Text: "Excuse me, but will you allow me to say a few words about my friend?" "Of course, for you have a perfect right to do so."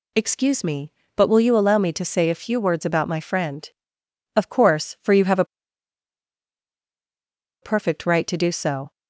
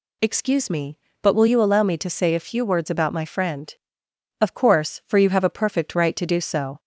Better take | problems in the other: second | pauses between "a" and "perfect"; strong; at 5.4 s; 2.1 s long

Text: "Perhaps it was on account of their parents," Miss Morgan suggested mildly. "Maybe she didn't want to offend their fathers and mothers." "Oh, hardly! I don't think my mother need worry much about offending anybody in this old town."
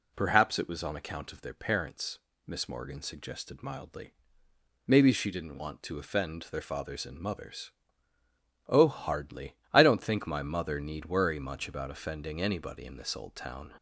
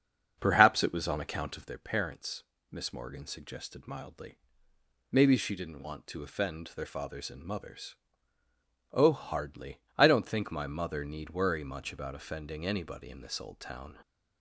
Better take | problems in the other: first | starts louder than the rest; until 1.8 s; 7 dB

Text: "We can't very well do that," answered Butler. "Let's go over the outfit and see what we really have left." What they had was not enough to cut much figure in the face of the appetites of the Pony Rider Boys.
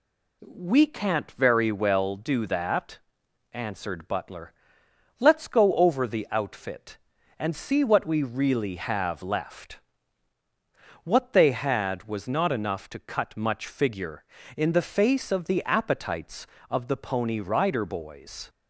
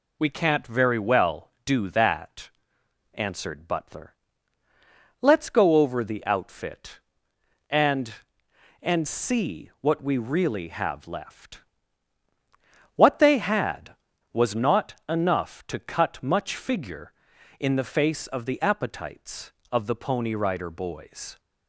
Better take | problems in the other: first | says "and" twice; at 8.8 s

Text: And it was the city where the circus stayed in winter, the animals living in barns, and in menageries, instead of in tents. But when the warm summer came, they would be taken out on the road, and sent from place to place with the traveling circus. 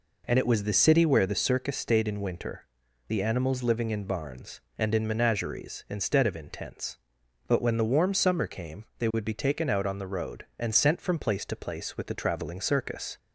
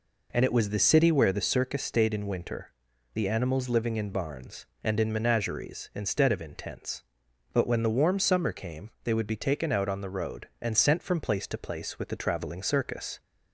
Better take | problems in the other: neither | none

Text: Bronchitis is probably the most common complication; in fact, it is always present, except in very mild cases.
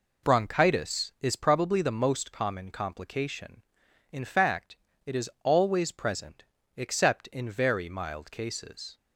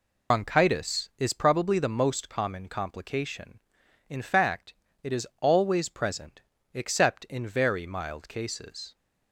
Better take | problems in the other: first | loses the start of "Bronchitis"; at 0.3 s; 85 ms

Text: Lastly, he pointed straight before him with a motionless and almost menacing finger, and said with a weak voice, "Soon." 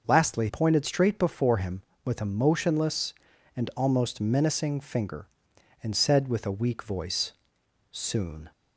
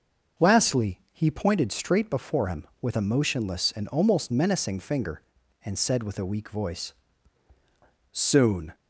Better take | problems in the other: second | starts louder than the rest; noticeable; until 1.0 s; 6 dB; noticeable in the second // skips "he"; at 0.4 s

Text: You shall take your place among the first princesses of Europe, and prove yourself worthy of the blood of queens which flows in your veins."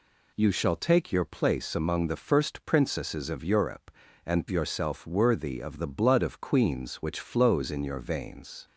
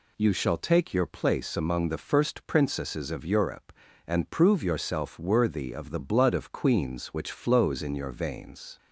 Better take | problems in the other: second | skips "prove"; at 4.4 s

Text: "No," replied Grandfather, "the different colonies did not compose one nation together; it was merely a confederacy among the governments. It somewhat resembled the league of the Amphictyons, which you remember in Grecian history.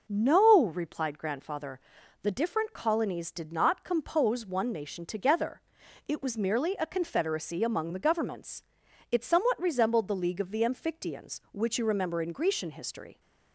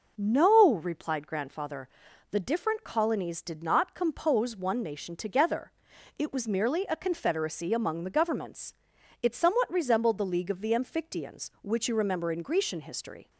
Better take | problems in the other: neither | none

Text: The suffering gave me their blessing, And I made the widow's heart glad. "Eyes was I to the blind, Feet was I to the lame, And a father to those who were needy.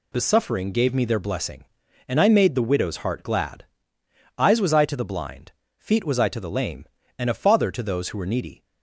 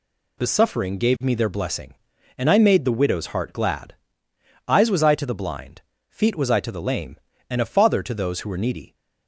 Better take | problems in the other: neither | none

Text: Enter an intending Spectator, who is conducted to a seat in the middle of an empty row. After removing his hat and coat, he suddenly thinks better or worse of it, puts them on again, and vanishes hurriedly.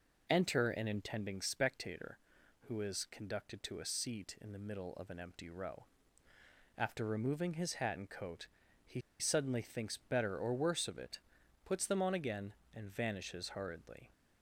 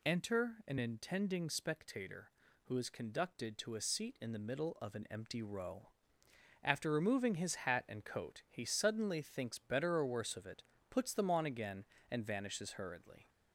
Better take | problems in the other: second | pauses between "he" and "suddenly"; slight; at 8.9 s; 0.20 s long

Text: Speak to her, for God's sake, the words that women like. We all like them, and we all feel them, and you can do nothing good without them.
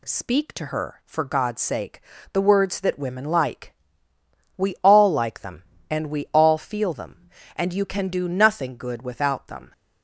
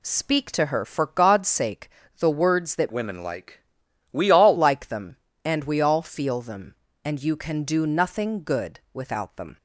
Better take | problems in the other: first | changes voice from "women" to "all"; from 2.9 to 4.5 s; 1.6 s long

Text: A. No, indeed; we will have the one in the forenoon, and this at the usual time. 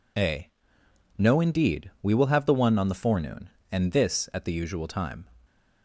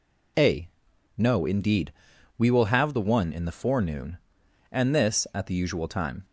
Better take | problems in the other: second | says "on" for "in"; at 2.7 s

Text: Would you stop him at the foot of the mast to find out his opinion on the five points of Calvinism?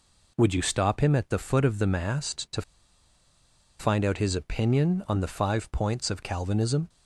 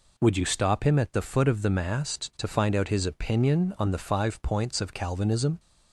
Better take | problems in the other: second | pauses between "to" and "find"; at 2.6 s; 1.1 s long

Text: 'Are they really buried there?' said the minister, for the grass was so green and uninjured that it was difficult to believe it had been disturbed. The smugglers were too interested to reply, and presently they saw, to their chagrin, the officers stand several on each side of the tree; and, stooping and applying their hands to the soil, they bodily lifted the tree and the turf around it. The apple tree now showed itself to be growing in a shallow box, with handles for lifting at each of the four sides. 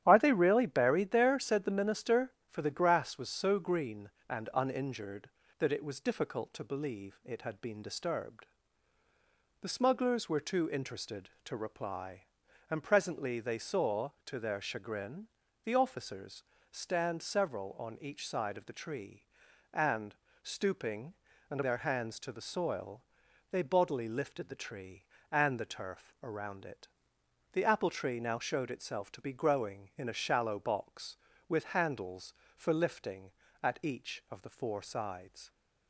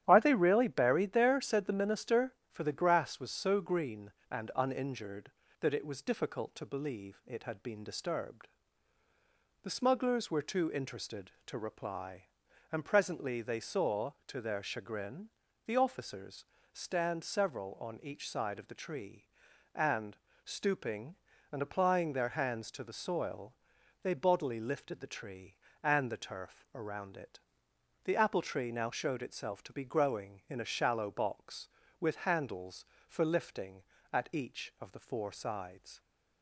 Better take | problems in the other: second | starts louder than the rest; strong; until 1.0 s; 11 dB; strong in the second // pauses between "officers" and "stand"; slight; at 16.4 s; 0.30 s long; slight in the second // skips "applying"; at 21.6 s

